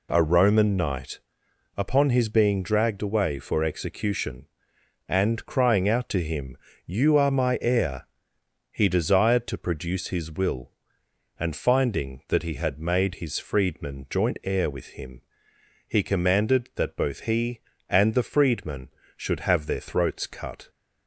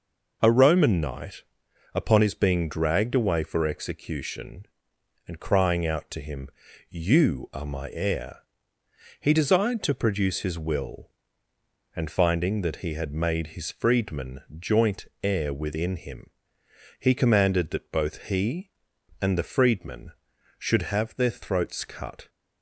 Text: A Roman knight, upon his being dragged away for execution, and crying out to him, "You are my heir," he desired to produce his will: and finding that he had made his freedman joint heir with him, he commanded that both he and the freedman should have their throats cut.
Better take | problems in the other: first | pauses between "freedman" and "joint"; slight; at 14.4 s; 0.16 s long // pauses between "joint" and "heir"; slight; at 15.0 s; 0.16 s long // says "within" for "with"; at 15.5 s

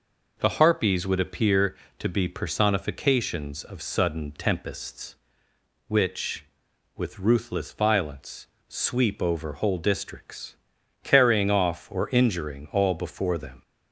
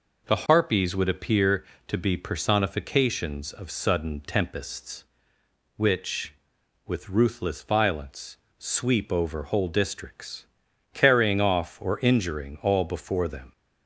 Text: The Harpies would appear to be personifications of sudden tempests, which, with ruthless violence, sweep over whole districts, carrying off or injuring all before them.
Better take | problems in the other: neither | none

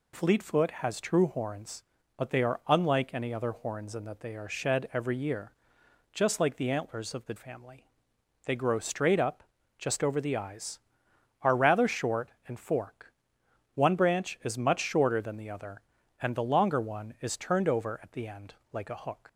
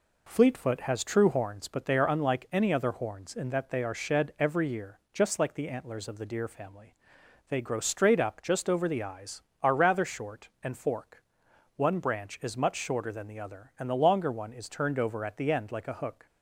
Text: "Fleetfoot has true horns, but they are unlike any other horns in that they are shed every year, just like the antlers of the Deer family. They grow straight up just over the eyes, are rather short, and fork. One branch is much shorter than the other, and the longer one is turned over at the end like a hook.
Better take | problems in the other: second | skips "Deer"; at 7.3 s // pauses between "up" and "just"; slight; at 9.4 s; 0.34 s long // pauses between "end" and "like"; slight; at 18.5 s; 0.16 s long

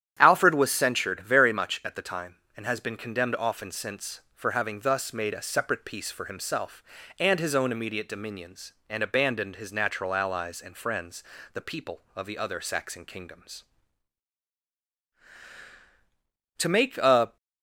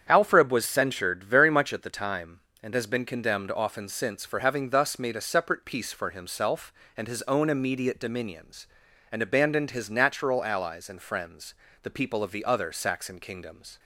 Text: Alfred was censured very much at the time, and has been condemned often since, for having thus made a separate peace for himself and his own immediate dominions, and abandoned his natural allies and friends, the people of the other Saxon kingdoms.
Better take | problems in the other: second | starts louder than the rest; strong; until 1.2 s; 10 dB; strong in the second // goes on to say "To make a"; noticeable; from 16.5 s on; 0.78 s long

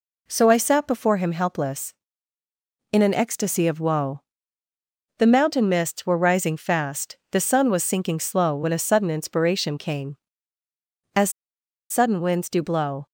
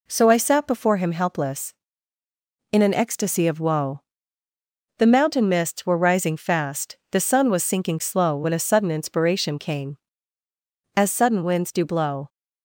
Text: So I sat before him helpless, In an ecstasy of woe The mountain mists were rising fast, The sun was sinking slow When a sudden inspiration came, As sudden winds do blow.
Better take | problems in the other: second | pauses between "woe" and "The"; noticeable; at 4.2 s; 0.96 s long; noticeable in the second // pauses between "As" and "sudden"; noticeable; at 11.2 s; 0.60 s long

